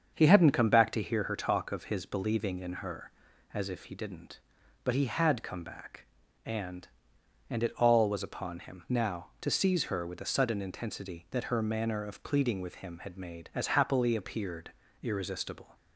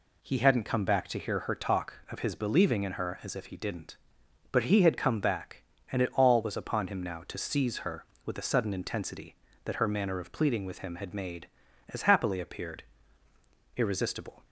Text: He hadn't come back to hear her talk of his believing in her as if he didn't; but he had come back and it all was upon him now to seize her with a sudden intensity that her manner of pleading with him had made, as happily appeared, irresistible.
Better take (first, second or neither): second